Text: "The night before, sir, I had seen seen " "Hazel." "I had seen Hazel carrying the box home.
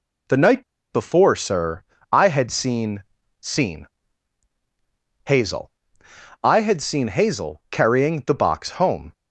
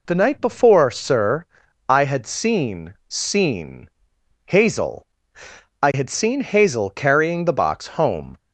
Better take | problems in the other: second | pauses between "night" and "before"; slight; at 0.6 s; 0.28 s long // pauses between "seen" and "seen"; slight; at 3.0 s; 0.36 s long

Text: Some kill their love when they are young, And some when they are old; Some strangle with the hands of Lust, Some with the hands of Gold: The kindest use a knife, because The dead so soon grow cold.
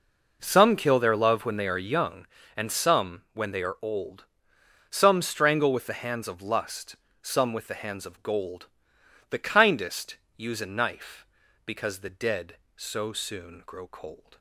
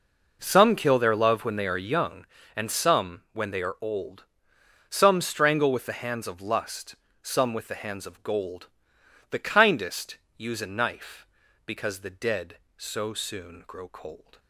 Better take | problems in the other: neither | pauses between "kindest" and "use"; slight; the same in both

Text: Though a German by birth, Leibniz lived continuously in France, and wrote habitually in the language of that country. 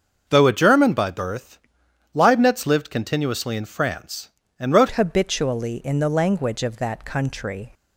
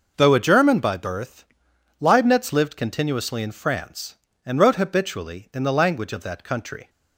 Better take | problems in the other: second | starts louder than the rest; until 1.2 s; 6.5 dB // changes voice at "habitually"; from 4.9 s on; 2.8 s long

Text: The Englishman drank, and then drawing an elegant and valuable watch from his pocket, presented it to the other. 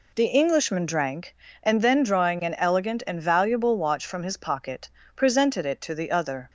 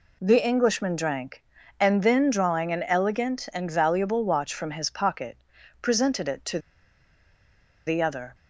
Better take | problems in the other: first | pauses between "to" and "the"; strong; at 6.5 s; 1.2 s long

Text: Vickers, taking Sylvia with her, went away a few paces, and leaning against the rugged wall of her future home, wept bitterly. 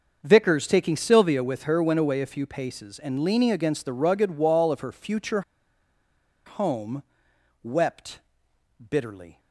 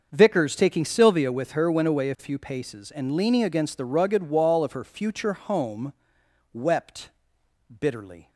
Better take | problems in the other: second | starts louder than the rest; until 1.2 s; 6.5 dB; also in the second // pauses between "future" and "home"; at 5.4 s; 1.0 s long // pauses between "wept" and "bitterly"; noticeable; at 8.1 s; 0.70 s long; noticeable in the second

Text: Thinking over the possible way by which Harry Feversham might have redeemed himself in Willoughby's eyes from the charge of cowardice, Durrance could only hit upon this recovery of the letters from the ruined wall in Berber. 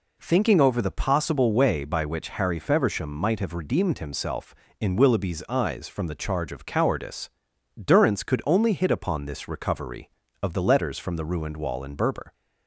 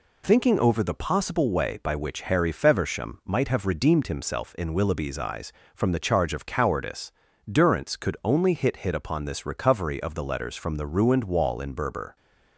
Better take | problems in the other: first | says "hit" twice; at 8.7 s

